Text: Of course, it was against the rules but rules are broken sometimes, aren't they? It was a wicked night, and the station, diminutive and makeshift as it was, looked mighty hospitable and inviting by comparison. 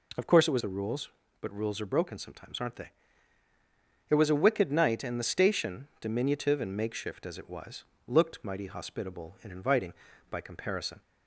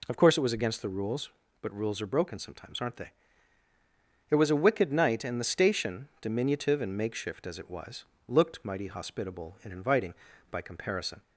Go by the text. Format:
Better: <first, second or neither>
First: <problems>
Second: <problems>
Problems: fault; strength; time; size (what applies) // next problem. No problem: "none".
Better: second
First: skips "against"; at 0.6 s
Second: none